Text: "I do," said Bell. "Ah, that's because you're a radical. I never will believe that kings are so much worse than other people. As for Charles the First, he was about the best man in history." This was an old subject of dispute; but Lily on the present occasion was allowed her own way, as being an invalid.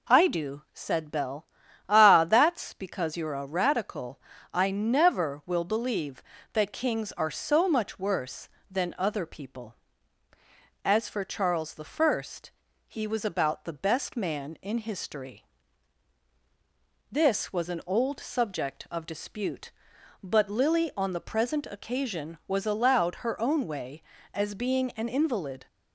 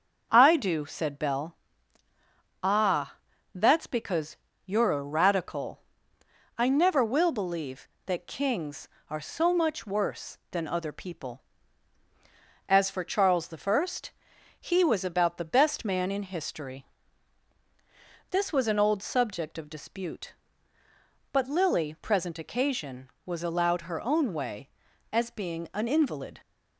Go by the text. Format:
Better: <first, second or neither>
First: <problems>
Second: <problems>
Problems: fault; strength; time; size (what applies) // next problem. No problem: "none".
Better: first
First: none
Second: starts louder than the rest; until 1.3 s; 6.5 dB // pauses between "because" and "you're"; slight; at 4.3 s; 0.28 s long // skips "on the"; at 21.9 s